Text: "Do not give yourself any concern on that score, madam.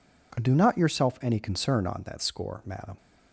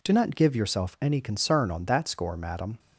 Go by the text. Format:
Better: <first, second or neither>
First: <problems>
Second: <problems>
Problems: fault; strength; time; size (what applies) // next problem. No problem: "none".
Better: second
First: skips "give"; at 0.7 s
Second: none